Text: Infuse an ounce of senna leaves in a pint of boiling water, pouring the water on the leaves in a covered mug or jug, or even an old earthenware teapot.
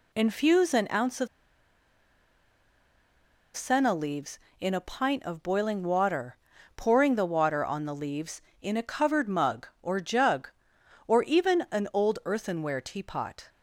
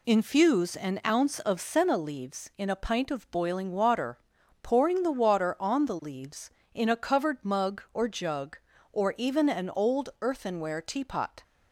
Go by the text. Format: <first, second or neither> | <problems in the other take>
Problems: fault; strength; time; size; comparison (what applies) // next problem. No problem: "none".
second | pauses between "of" and "senna"; strong; at 1.2 s; 2.2 s long